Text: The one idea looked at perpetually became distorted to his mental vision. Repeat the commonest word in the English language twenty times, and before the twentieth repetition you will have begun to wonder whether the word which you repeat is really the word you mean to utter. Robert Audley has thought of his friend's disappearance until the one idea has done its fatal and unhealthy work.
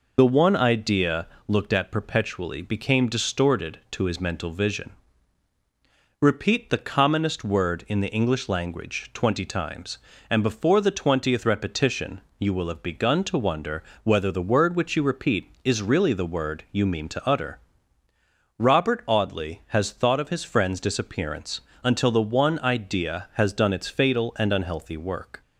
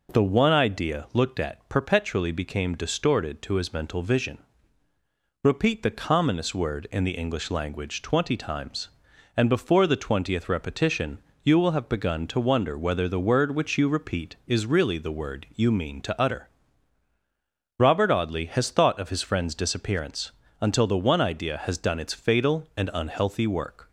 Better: second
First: loses the start of "The"; at 0.1 s; 55 ms // pauses between "idea" and "looked"; slight; at 1.2 s; 0.20 s long // pauses between "repetition" and "you"; slight; at 12.1 s; 0.20 s long // pauses between "wonder" and "whether"; slight; at 13.8 s; 0.18 s long // pauses between "disappearance" and "until"; slight; at 21.6 s; 0.24 s long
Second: pauses between "repetition" and "you"; slight; at 11.2 s; 0.24 s long // pauses between "disappearance" and "until"; slight; at 20.3 s; 0.28 s long

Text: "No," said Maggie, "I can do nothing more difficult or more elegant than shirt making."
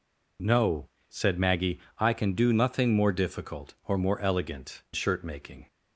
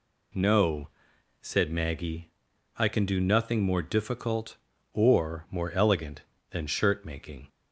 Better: second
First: skips "than"; at 4.8 s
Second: none

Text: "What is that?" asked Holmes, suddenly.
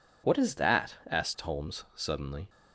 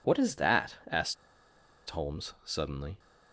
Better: first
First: none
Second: pauses between "asked" and "Holmes"; noticeable; at 1.1 s; 0.73 s long

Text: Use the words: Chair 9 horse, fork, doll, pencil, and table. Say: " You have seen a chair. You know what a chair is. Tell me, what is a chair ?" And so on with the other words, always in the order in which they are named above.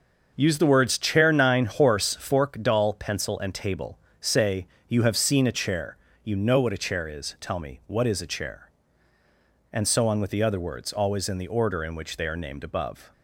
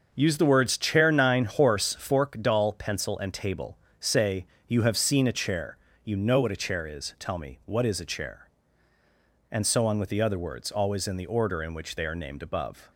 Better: neither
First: starts louder than the rest; until 1.3 s; 7 dB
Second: starts louder than the rest; strong; until 1.1 s; 7 dB

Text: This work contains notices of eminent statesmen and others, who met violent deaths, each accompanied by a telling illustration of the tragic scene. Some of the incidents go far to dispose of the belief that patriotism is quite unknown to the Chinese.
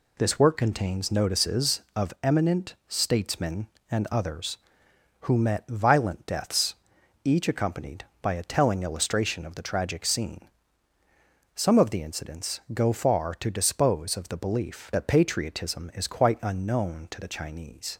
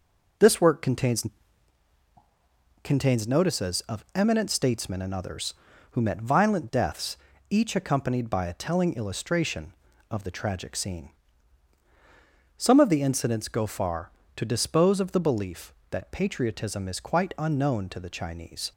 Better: first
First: none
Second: says "contains" twice; at 2.8 s

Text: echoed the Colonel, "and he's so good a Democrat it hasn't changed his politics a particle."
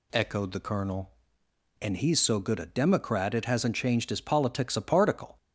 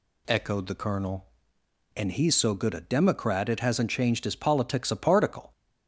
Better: neither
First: none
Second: none

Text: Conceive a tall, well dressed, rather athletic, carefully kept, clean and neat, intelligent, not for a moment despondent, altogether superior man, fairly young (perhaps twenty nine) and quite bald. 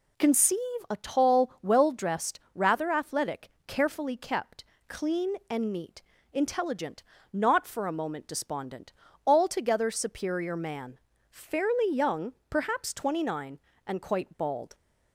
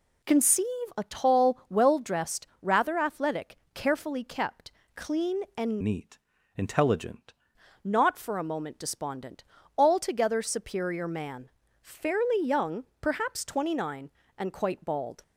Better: first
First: pauses between "Conceive" and "a"; slight; at 0.5 s; 0.30 s long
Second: pauses between "Conceive" and "a"; slight; at 0.6 s; 0.30 s long // changes voice from "neat" to "intelligent"; from 5.8 to 7.3 s; 1.5 s long

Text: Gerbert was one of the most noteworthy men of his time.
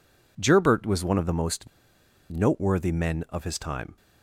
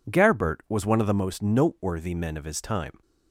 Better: second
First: pauses between "most" and "noteworthy"; noticeable; at 1.6 s; 0.62 s long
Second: none

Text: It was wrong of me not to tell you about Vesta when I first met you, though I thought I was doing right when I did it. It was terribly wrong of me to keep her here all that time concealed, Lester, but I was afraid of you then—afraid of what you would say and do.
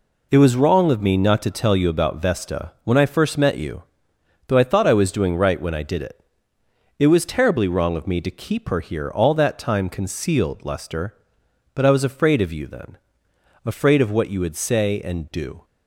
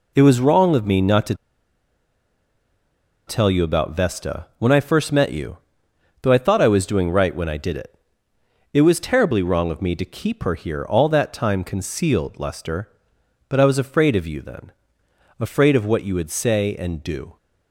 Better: first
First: none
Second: pauses between "to" and "tell"; strong; at 1.3 s; 1.9 s long

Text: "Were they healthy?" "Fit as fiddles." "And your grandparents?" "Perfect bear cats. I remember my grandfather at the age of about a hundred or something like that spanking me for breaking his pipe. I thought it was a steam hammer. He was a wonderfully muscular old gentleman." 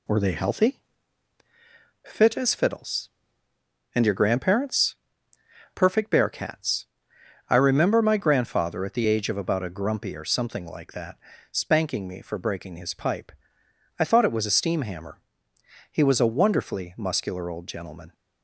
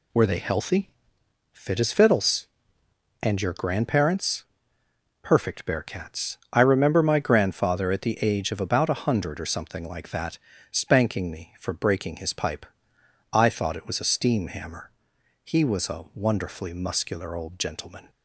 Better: second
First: says "grumpy" for "hundred"; at 9.6 s // pauses between "that" and "spanking"; slight; at 11.1 s; 0.32 s long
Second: pauses between "that" and "spanking"; slight; at 10.3 s; 0.34 s long

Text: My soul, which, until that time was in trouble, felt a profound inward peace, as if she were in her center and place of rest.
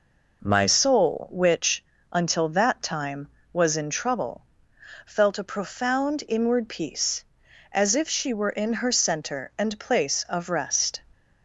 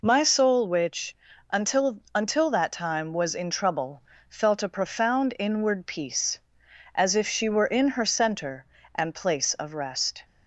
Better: first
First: none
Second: says "until" twice; at 2.1 s

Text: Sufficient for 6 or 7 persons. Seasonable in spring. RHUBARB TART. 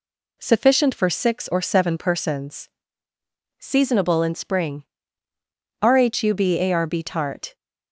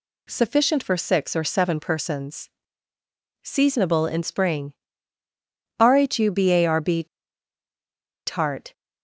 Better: first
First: none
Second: pauses between "RHUBARB" and "TART"; at 7.0 s; 1.2 s long

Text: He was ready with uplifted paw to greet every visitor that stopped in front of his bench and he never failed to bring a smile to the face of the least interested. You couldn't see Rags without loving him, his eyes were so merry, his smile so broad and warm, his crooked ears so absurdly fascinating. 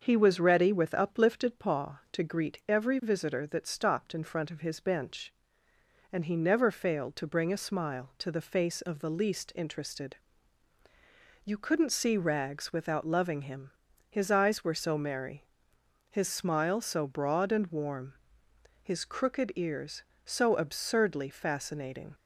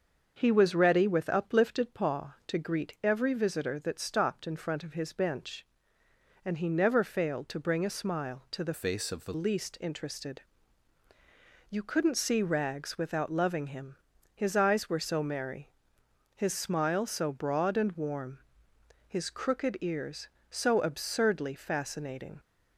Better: first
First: starts louder than the rest; until 1.0 s; 6.5 dB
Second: starts louder than the rest; until 1.3 s; 6.5 dB // changes voice from "face" to "the"; from 8.7 to 9.3 s; 0.6 s long

